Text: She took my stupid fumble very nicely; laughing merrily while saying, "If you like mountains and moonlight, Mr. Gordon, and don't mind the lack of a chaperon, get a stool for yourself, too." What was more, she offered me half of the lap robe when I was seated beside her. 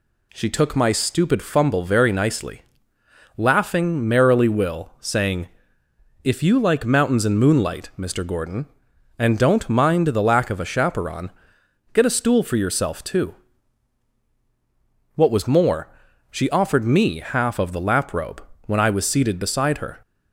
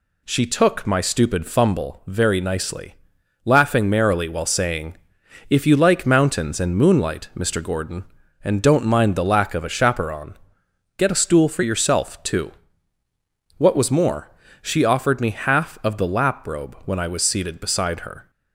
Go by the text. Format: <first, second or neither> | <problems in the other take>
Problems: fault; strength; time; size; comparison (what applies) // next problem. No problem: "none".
second | says "will" for "while"; at 4.4 s // pauses between "robe" and "when"; slight; at 18.4 s; 0.24 s long